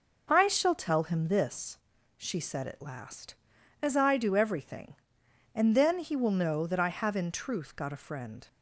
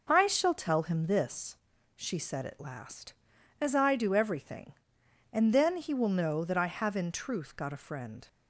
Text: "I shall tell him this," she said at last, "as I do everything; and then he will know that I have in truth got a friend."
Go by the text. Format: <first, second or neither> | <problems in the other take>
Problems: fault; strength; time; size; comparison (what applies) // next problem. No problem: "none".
neither | none